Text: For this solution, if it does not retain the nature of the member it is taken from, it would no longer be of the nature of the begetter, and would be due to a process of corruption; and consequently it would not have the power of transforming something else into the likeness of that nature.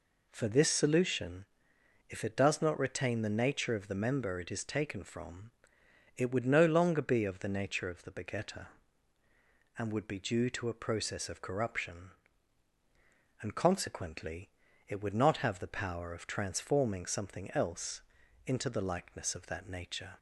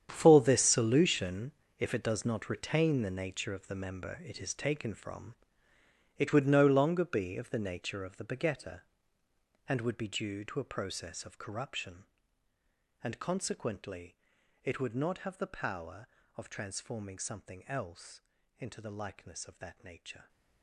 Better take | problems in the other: first | gets quieter; strong; throughout; 14 dB // pauses between "consequently" and "it"; at 14.1 s; 0.44 s long; also in the first // pauses between "else" and "into"; at 18.1 s; 0.38 s long; also in the first

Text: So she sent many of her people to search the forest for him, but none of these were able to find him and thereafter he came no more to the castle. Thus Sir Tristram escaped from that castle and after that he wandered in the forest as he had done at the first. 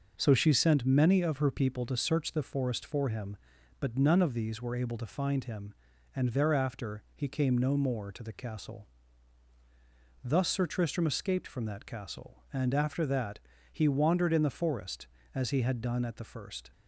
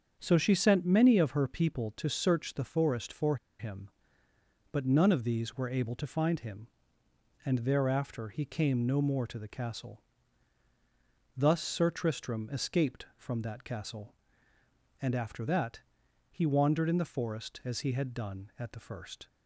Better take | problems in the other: first | starts louder than the rest; strong; until 1.2 s; 7 dB // pauses between "for" and "him"; slight; at 3.3 s; 0.23 s long // pauses between "that" and "he"; noticeable; at 15.8 s; 0.50 s long; slight in the first

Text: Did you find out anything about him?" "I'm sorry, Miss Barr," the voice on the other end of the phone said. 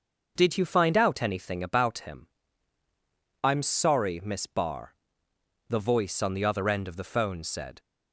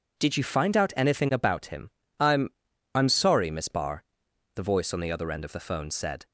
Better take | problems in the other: first | says "I'm" twice; at 2.9 s

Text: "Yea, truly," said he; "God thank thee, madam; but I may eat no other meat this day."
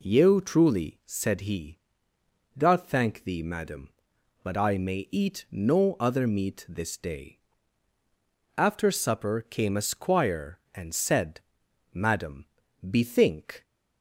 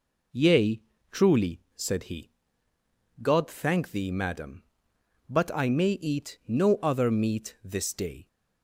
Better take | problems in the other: second | goes on to say "After supper came a squire and said Madam bethink"; strong; from 8.5 s on; 5.0 s long

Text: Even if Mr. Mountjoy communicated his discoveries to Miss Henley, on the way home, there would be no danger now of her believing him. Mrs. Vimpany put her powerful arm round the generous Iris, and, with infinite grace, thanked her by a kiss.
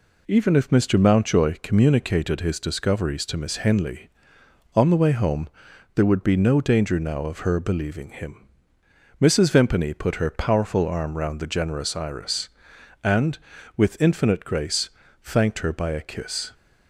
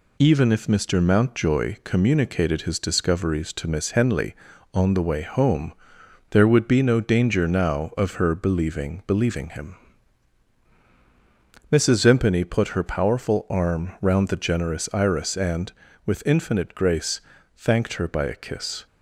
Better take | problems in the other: first | says "believing" twice; at 9.0 s

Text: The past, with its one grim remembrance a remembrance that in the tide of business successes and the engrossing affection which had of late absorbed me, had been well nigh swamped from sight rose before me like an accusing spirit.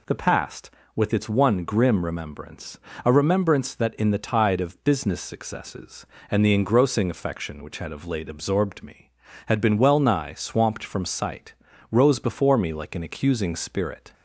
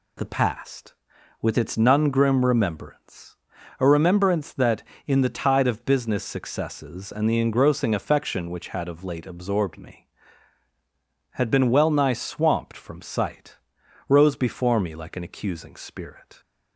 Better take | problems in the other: first | says "none" for "one"; at 1.7 s // pauses between "remembrance" and "a"; at 3.3 s; 0.43 s long; slight in the first // pauses between "sight" and "rose"; noticeable; at 13.5 s; 0.50 s long; also in the first

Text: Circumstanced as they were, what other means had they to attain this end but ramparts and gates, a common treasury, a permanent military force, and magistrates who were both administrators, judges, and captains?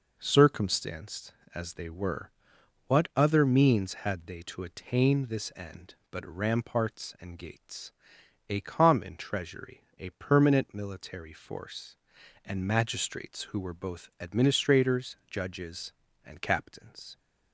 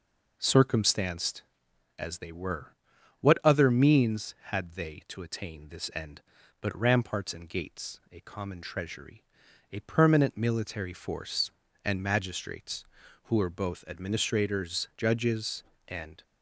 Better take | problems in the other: first | stops before "captains"; at 16.2 s

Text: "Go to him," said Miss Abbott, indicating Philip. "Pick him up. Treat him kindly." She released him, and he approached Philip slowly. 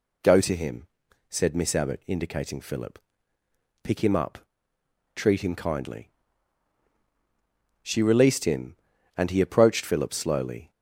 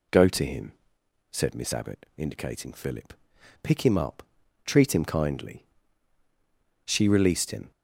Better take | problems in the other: first | stops before "and he approached Philip slowly"; at 7.7 s

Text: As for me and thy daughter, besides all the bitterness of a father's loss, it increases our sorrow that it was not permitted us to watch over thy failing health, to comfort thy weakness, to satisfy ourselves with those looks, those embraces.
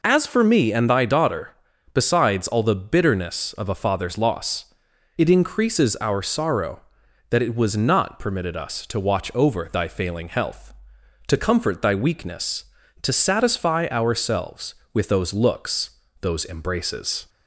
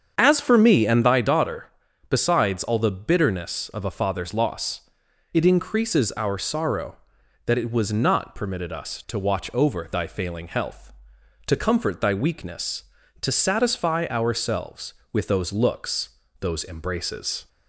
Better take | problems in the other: first | starts louder than the rest; strong; until 1.3 s; 7.5 dB

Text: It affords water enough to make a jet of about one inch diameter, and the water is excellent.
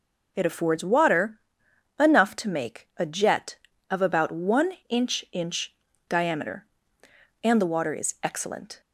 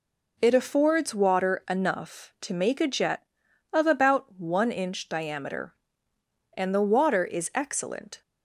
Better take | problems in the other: second | pauses between "water" and "enough"; noticeable; at 1.3 s; 0.60 s long // pauses between "one" and "inch"; slight; at 4.7 s; 0.16 s long // says "inch" twice; at 5.3 s

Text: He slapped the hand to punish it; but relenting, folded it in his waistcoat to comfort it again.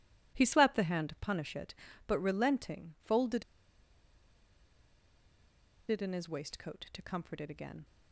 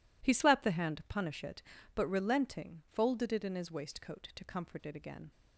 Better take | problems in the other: second | pauses between "folded" and "it"; strong; at 3.4 s; 2.4 s long

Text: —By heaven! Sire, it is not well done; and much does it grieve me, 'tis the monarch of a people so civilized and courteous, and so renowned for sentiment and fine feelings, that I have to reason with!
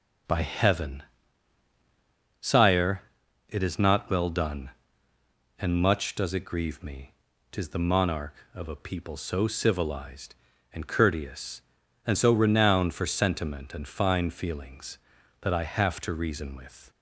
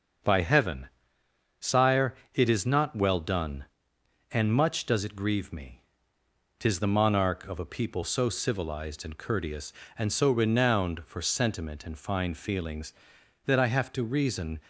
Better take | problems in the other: first | starts louder than the rest; until 1.9 s; 6.5 dB; noticeable in the first // stops before "with"; at 14.6 s

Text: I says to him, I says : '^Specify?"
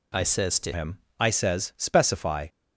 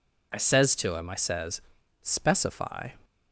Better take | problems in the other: second | changes voice at "him"; from 0.7 s on; 1.7 s long

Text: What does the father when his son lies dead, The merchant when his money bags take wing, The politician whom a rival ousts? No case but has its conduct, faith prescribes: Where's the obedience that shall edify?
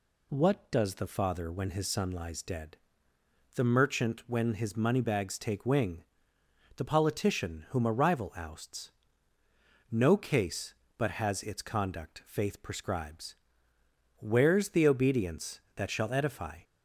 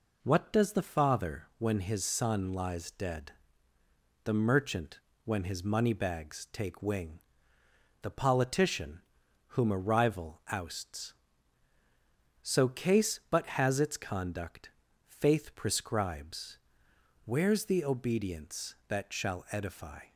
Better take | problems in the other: first | pauses between "merchant" and "when"; slight; at 5.0 s; 0.24 s long // pauses between "politician" and "whom"; noticeable; at 9.0 s; 0.54 s long // says "So" for "No"; at 12.4 s

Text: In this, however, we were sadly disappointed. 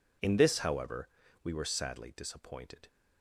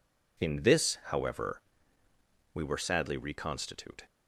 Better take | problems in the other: first | says "reconstitute" for "disappointed"; at 3.1 s

